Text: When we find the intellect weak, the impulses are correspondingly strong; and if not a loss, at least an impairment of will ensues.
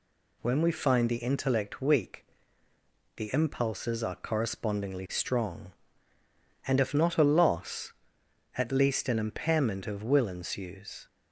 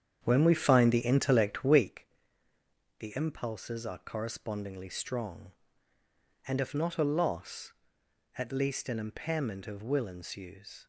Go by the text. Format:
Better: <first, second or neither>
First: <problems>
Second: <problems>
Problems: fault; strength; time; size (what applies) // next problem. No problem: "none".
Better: first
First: none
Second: starts louder than the rest; strong; until 2.0 s; 8.5 dB